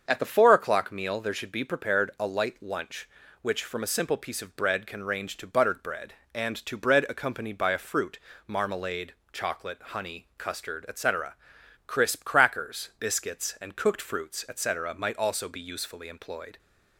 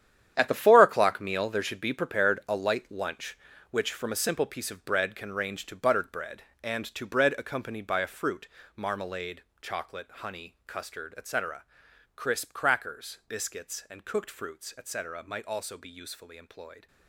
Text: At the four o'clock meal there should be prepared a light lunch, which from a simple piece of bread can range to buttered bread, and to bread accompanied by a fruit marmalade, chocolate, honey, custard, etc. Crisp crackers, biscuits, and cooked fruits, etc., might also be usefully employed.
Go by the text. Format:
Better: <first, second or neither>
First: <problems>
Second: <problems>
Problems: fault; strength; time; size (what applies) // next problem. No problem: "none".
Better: first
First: starts louder than the rest; until 1.0 s; 7 dB // pauses between "fruit" and "marmalade"; slight; at 8.1 s; 0.26 s long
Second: gets quieter; strong; throughout; 12.5 dB // starts louder than the rest; strong; until 1.3 s; 10 dB // pauses between "fruit" and "marmalade"; slight; at 8.4 s; 0.26 s long